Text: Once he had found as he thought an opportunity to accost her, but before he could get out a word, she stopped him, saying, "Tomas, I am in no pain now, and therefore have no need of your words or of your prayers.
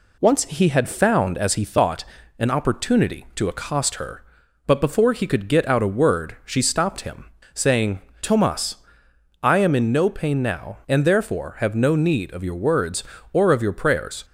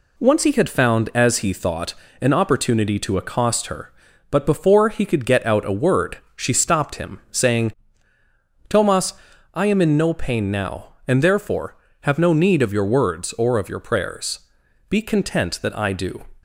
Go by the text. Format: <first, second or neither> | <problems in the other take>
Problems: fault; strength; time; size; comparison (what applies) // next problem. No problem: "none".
first | pauses between "thought" and "an"; slight; at 1.9 s; 0.26 s long; slight in the first // goes on to say "Be content that I do"; from 14.8 s on; 1.3 s long